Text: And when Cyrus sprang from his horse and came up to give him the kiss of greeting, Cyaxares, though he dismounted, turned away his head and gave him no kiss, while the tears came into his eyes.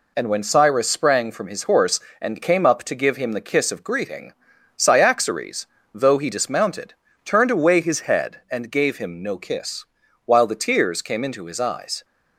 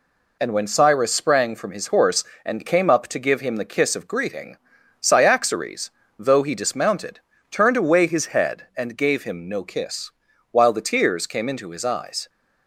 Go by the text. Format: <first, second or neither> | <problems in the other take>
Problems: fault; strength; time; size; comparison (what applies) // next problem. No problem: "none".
neither | none